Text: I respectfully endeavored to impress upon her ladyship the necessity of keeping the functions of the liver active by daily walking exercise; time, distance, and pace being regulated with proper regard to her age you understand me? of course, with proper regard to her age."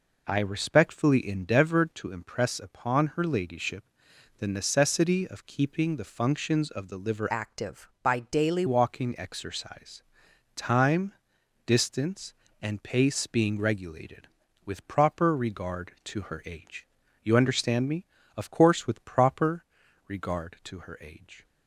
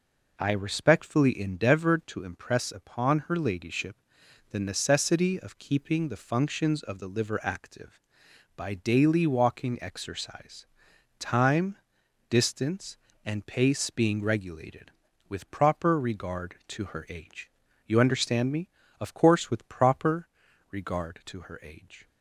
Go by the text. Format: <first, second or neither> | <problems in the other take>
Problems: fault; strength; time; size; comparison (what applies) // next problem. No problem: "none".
second | pauses between "ladyship" and "the"; noticeable; at 3.8 s; 0.56 s long; noticeable in the second // changes voice from "active" to "daily"; from 7.2 to 8.6 s; 1.4 s long // pauses between "age" and "you"; slight; at 16.8 s; 0.34 s long; slight in the second // pauses between "proper" and "regard"; at 19.6 s; 0.44 s long; also in the second